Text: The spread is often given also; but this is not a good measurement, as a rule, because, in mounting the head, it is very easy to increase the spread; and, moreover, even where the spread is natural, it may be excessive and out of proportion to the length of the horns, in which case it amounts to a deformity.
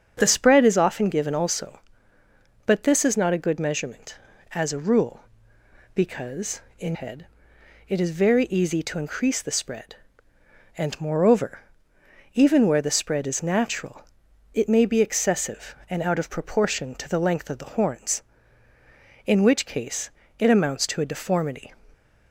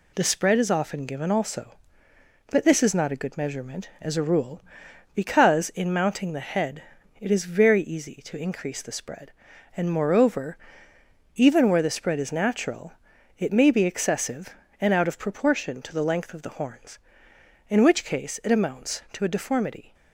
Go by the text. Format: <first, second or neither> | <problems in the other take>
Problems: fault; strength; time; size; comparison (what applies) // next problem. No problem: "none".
second | starts louder than the rest; until 1.1 s; 7 dB // skips "mounting the"; at 6.9 s // pauses between "case" and "it"; slight; at 20.1 s; 0.26 s long